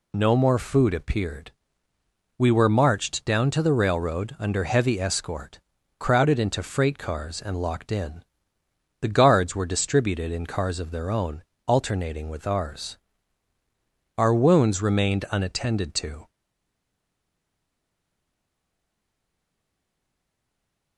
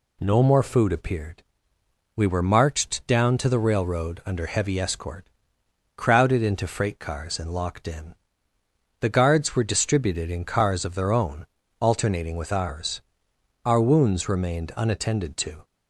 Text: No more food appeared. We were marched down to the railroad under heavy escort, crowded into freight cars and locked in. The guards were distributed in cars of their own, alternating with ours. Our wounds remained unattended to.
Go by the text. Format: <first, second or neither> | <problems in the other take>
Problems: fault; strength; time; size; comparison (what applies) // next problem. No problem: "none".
second | stays silent after the last word; strong; from 16.2 s on; 4.7 s long